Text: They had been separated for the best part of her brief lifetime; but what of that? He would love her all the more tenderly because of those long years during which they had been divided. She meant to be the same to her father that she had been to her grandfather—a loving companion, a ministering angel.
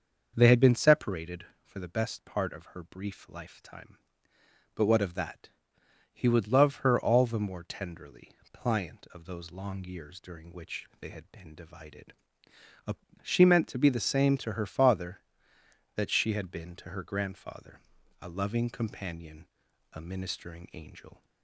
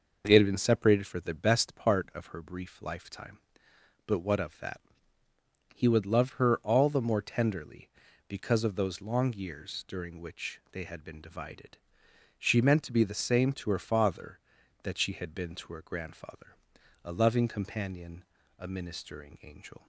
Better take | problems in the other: second | starts louder than the rest; until 1.3 s; 6.5 dB // says "pliant" for "because"; at 8.5 s

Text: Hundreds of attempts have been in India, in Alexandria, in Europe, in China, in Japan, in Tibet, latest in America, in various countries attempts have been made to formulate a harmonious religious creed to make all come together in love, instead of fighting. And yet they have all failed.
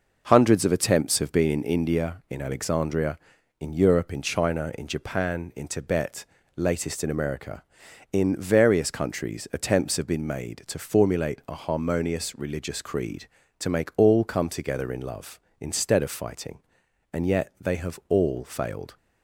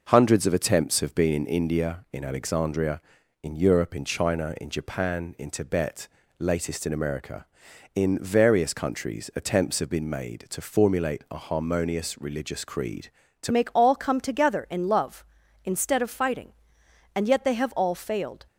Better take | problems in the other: first | changes voice at "make"; from 13.5 s on; 4.9 s long

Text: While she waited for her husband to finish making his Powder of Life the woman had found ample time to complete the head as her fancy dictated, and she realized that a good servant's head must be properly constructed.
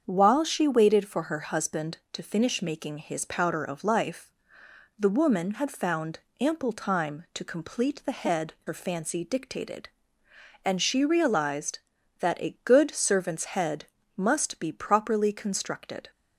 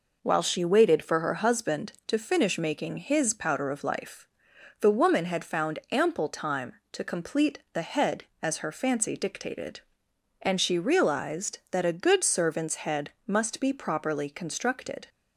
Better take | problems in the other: second | starts louder than the rest; strong; until 1.0 s; 7.5 dB // pauses between "Life" and "the"; noticeable; at 4.2 s; 0.70 s long; noticeable in the second // pauses between "found" and "ample"; slight; at 6.1 s; 0.20 s long // skips "as"; at 8.5 s // pauses between "head" and "must"; slight; at 13.8 s; 0.30 s long; slight in the second

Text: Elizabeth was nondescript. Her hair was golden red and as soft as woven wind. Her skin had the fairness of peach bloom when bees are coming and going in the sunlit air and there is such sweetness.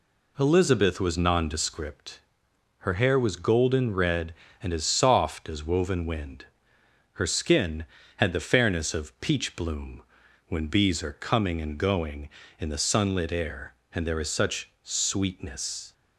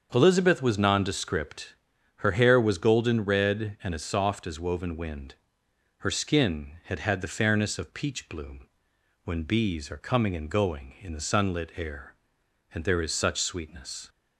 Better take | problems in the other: first | starts louder than the rest; until 1.1 s; 7 dB // says "had" twice; at 7.0 s // pauses between "bloom" and "when"; noticeable; at 8.6 s; 0.56 s long; noticeable in the first

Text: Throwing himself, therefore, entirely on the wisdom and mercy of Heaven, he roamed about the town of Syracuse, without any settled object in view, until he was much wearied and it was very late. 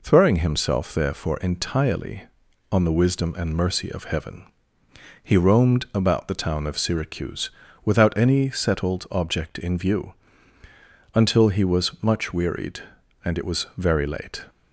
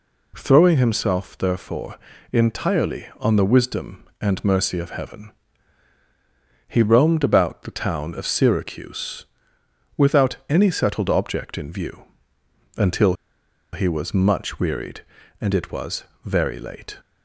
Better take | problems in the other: first | pauses between "until" and "he"; noticeable; at 13.1 s; 0.58 s long // pauses between "was" and "very"; slight; at 16.0 s; 0.20 s long

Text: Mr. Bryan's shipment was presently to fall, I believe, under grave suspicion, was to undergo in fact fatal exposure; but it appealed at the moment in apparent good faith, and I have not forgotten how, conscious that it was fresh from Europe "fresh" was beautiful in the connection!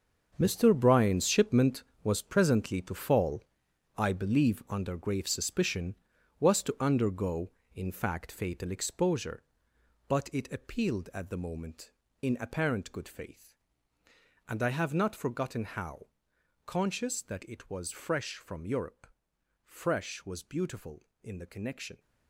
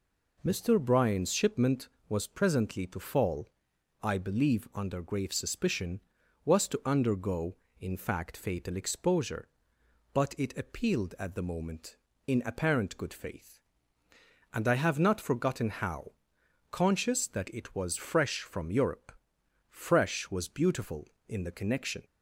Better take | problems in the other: second | gets quieter; strong; throughout; 12 dB // pauses between "Europe" and "fresh"; noticeable; at 19.0 s; 0.56 s long; noticeable in the second

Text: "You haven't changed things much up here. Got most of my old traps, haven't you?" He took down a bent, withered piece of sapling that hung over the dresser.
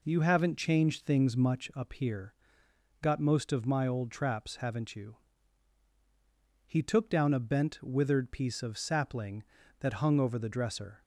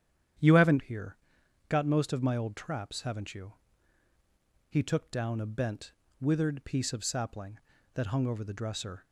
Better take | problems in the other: first | starts louder than the rest; strong; until 1.9 s; 9.5 dB // skips "changed things much up"; at 0.8 s

